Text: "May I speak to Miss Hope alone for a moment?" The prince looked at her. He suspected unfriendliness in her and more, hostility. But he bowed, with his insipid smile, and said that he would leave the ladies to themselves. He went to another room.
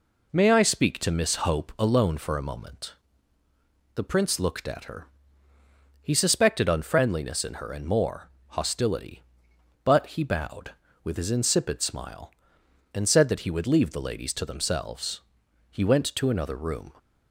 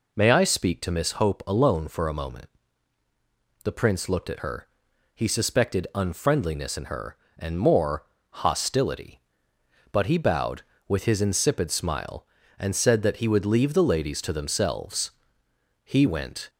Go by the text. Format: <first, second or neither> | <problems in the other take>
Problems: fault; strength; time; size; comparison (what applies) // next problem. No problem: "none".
first | stops before "to another room"; at 16.4 s